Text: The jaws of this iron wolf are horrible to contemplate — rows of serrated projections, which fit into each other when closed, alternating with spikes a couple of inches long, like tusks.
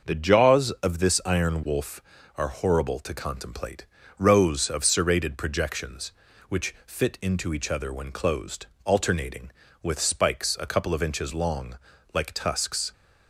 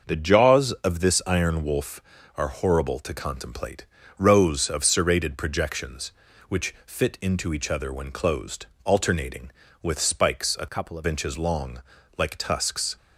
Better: first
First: none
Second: changes voice from "couple" to "of"; from 10.6 to 11.0 s; 0.4 s long

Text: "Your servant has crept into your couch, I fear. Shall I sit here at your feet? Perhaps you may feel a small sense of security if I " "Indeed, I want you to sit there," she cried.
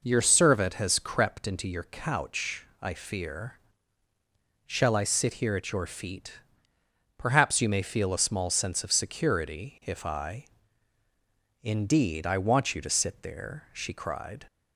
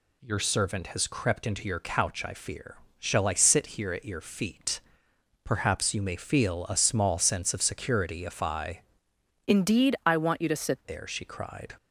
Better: first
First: none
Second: changes voice from "Indeed" to "sit"; from 9.4 to 10.8 s; 1.4 s long

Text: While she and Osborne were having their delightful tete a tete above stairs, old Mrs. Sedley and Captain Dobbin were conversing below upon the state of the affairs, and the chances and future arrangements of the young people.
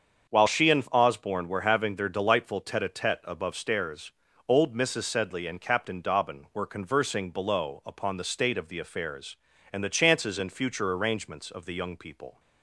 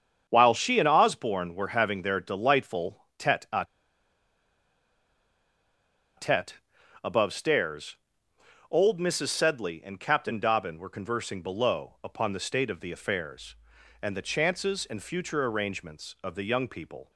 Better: first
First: starts louder than the rest; until 1.3 s; 7 dB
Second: starts louder than the rest; strong; until 1.3 s; 7.5 dB // pauses between "a" and "tete"; strong; at 3.6 s; 2.5 s long // pauses between "tete" and "above"; noticeable; at 6.5 s; 0.48 s long

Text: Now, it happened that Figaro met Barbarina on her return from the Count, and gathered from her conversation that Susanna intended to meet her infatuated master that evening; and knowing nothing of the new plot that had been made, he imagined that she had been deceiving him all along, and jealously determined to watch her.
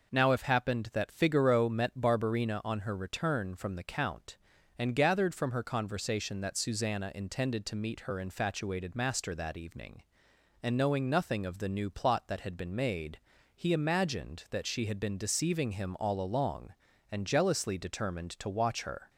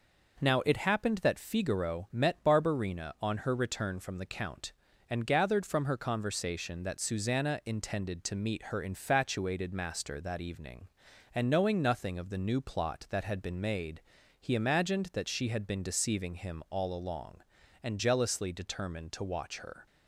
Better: second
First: says "if" for "it"; at 0.3 s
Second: none

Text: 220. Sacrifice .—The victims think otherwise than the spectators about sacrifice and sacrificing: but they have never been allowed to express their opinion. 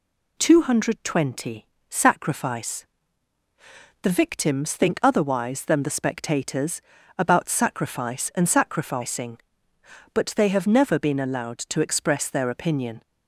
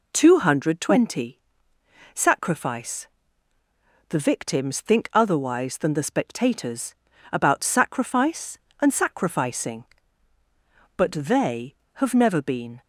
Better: first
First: pauses between "spectators" and "about"; at 6.7 s; 0.38 s long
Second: pauses between "spectators" and "about"; slight; at 6.9 s; 0.36 s long // stops before "allowed to express their opinion"; at 12.8 s

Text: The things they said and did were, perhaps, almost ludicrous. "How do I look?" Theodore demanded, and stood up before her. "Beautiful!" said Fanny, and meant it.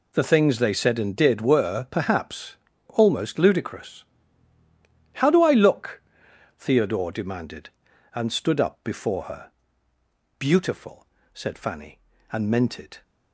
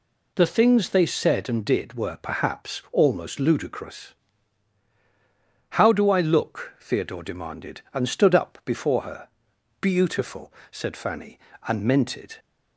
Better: neither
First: none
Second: none

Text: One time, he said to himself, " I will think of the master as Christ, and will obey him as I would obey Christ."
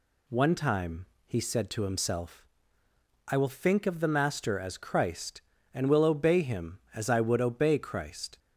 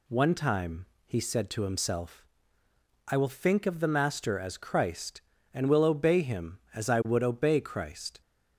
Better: neither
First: none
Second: none

